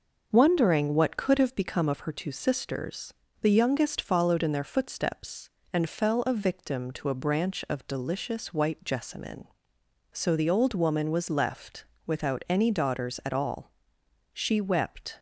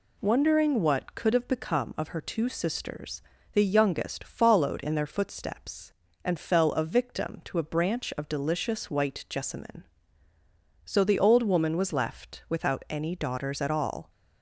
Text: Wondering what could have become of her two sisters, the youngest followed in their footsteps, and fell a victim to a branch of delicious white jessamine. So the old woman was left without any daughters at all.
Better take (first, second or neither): second